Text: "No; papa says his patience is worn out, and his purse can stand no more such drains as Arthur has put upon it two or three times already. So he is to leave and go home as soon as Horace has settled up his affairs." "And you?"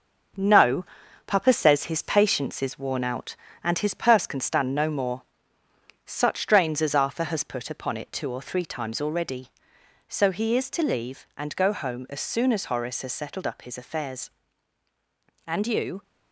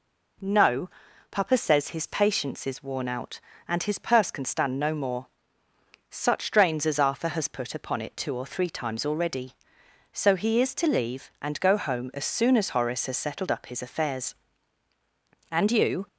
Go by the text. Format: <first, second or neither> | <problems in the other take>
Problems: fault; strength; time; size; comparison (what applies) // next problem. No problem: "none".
second | gets quieter; noticeable; throughout; 5 dB // pauses between "more" and "such"; noticeable; at 5.2 s; 0.82 s long; noticeable in the second